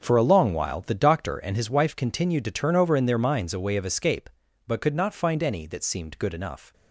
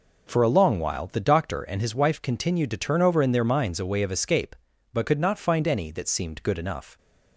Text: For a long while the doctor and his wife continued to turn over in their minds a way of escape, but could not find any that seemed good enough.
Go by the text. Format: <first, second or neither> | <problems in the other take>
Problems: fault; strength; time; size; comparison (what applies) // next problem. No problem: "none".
second | gets quieter; strong; throughout; 11.5 dB